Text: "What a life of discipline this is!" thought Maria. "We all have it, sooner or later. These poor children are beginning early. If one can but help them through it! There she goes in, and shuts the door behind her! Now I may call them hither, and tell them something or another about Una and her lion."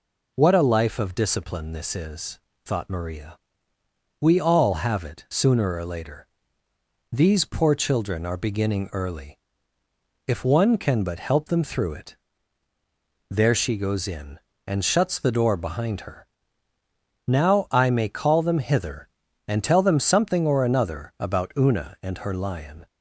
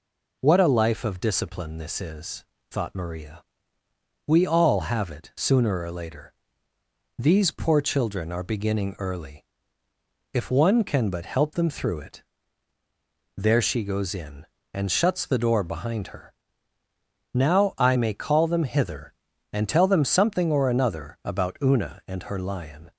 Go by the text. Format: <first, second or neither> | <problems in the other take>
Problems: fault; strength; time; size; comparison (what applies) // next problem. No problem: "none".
neither | none